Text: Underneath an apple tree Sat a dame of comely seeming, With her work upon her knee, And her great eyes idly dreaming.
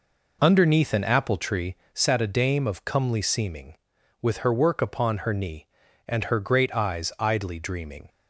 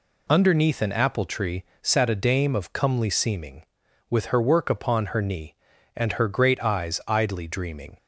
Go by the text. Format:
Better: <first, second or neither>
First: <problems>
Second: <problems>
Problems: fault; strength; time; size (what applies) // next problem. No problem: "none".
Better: second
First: starts louder than the rest; noticeable; until 1.7 s; 4.5 dB // pauses between "tree" and "Sat"; slight; at 1.7 s; 0.18 s long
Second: pauses between "tree" and "Sat"; slight; at 1.6 s; 0.18 s long